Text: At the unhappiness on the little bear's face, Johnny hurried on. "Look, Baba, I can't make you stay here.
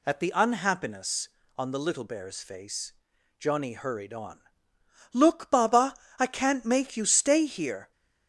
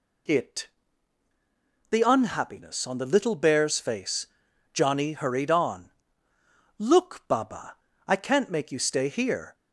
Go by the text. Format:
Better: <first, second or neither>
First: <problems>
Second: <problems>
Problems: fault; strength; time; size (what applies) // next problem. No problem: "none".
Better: first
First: none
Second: says "It" for "At"; at 0.2 s